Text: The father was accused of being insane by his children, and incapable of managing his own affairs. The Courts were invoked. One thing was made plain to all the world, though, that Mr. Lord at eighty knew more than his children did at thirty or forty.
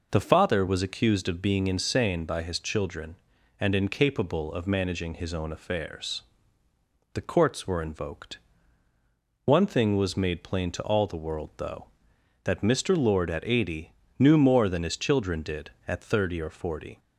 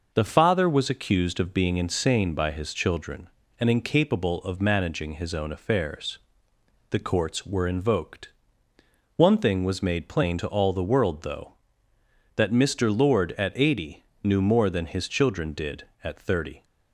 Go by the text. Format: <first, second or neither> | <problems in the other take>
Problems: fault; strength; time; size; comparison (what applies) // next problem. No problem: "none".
first | pauses between "eighty" and "knew"; slight; at 14.0 s; 0.20 s long; slight in the first // stops before "or forty"; at 16.6 s